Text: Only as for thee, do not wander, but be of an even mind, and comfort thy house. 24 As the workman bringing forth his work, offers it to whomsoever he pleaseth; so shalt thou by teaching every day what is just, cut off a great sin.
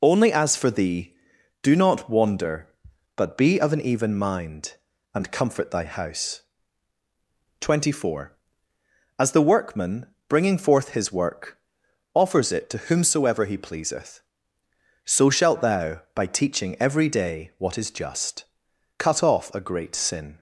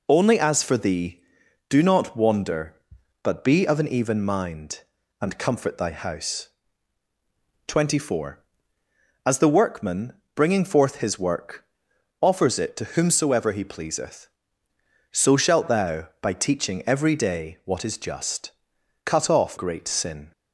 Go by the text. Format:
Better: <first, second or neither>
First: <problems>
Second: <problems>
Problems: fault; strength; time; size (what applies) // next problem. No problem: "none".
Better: first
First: pauses between "workman" and "bringing"; slight; at 10.0 s; 0.22 s long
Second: pauses between "workman" and "bringing"; slight; at 10.1 s; 0.22 s long // skips "a"; at 19.5 s